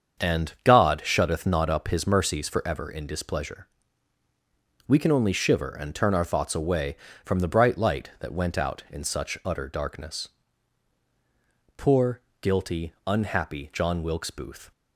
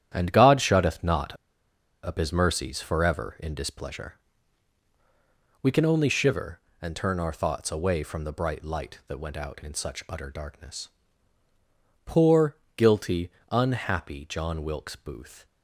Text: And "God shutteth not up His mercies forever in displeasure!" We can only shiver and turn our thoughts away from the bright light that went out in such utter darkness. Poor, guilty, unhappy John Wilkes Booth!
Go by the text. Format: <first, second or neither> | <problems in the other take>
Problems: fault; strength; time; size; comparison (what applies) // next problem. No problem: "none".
first | starts louder than the rest; strong; until 1.1 s; 10 dB; strong in the first // pauses between "not" and "up"; noticeable; at 1.3 s; 0.68 s long